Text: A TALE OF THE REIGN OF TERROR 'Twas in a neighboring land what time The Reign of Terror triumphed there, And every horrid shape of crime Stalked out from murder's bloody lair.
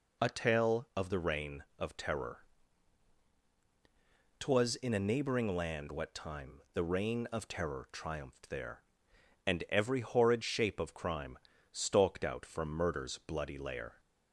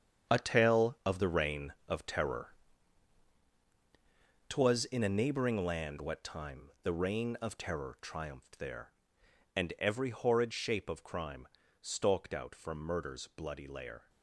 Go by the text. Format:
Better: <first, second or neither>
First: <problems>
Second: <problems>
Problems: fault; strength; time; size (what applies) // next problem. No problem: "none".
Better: first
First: pauses between "TERROR" and "Twas"; strong; at 2.3 s; 2.0 s long // pauses between "crime" and "Stalked"; slight; at 11.3 s; 0.34 s long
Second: gets quieter; strong; throughout; 11 dB // pauses between "TERROR" and "Twas"; strong; at 2.4 s; 2.0 s long // pauses between "crime" and "Stalked"; slight; at 11.4 s; 0.34 s long